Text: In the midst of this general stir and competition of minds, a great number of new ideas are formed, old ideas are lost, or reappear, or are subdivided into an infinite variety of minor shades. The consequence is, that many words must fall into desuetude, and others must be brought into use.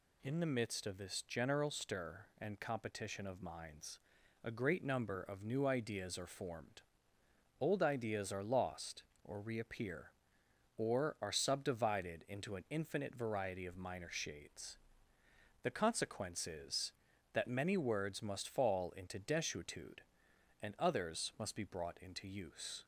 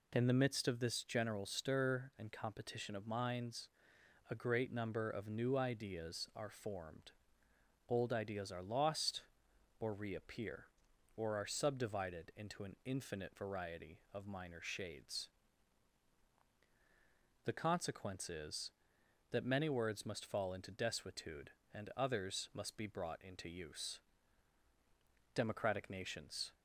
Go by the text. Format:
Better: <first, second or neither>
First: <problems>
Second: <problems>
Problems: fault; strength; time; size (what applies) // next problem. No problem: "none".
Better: first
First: none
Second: goes on to say "Democratic nations"; noticeable; from 25.3 s on; 1.2 s long